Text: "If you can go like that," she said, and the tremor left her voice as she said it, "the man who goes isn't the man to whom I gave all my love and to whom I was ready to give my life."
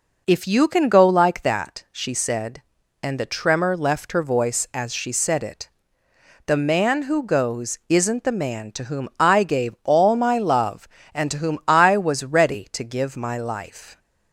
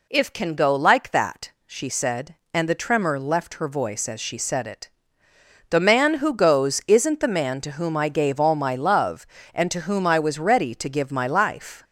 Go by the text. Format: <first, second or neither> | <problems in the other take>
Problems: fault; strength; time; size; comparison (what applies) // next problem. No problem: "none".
first | skips "you"; at 0.3 s